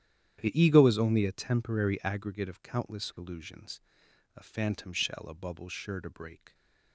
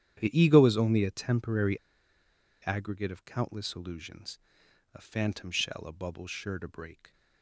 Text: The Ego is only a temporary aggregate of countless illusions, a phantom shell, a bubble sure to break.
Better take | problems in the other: first | starts louder than the rest; strong; until 1.2 s; 10.5 dB; strong in the first // pauses between "temporary" and "aggregate"; noticeable; at 1.7 s; 0.86 s long

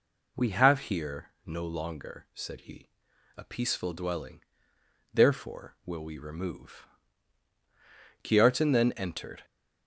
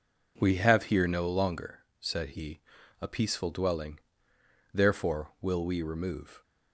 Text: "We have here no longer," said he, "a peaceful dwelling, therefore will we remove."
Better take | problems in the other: second | pauses between "here" and "no"; slight; at 1.3 s; 0.16 s long // goes on to say "Kiartan then entered"; noticeable; from 8.2 s on; 1.2 s long

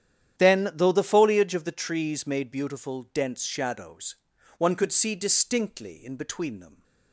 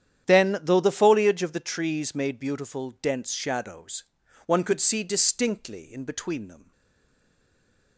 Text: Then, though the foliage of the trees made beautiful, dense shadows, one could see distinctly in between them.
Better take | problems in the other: first | starts louder than the rest; strong; until 1.3 s; 10 dB; strong in the first // stays silent after the last word; noticeable; from 6.7 s on; 1.2 s long

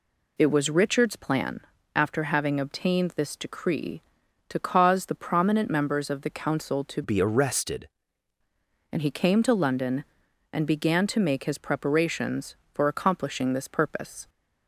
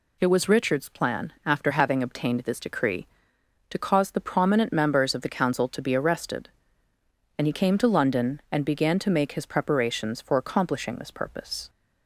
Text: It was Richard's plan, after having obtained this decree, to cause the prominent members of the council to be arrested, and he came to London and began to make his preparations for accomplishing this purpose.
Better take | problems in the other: second | changes voice from "be" to "arrested"; from 7.0 to 7.8 s; 0.8 s long

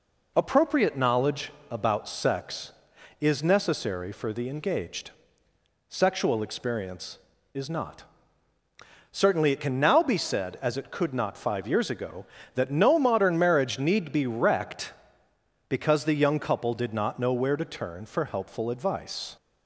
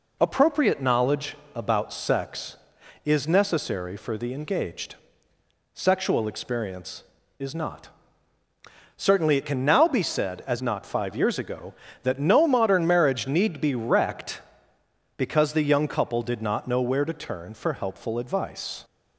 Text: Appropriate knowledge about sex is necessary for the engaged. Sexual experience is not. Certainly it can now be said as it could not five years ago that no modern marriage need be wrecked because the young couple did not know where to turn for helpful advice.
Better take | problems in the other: first | pauses between "knowledge" and "about"; slight; at 1.3 s; 0.18 s long; slight in the first // skips "it could"; at 10.6 s

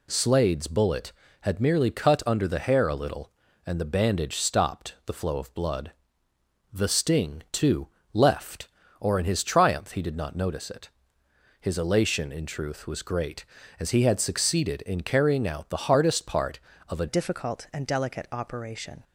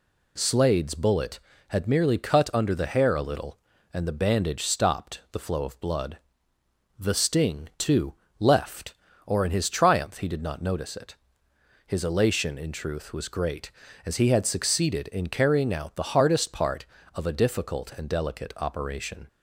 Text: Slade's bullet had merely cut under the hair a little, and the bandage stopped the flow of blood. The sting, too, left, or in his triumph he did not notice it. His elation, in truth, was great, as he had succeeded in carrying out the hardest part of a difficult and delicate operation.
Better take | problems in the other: second | changes voice at "difficult"; from 17.0 s on; 2.0 s long

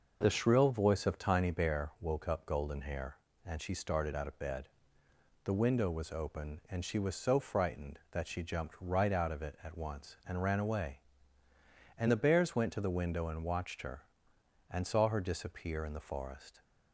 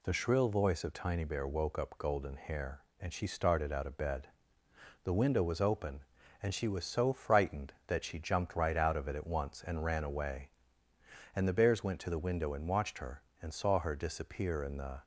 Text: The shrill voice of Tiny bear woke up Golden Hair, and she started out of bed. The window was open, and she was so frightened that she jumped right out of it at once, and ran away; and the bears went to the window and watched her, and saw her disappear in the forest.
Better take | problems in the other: first | stops before "forest"; at 15.0 s

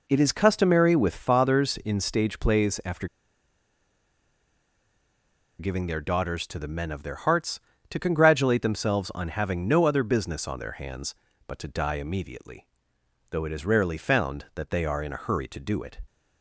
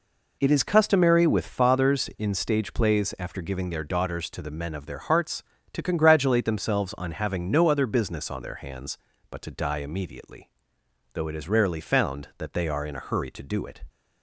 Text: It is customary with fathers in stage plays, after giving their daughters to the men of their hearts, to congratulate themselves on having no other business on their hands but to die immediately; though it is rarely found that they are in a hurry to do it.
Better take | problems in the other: second | pauses between "after" and "giving"; strong; at 3.0 s; 2.5 s long

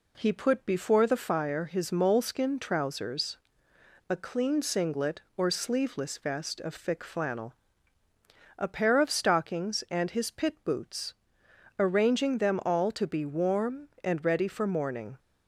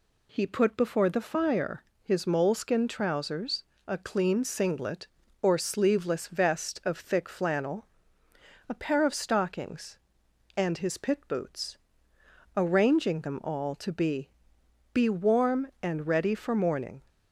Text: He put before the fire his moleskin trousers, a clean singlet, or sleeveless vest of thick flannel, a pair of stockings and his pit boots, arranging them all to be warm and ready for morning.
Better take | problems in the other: first | pauses between "fire" and "his"; slight; at 1.8 s; 0.22 s long // says "be" twice; at 14.9 s

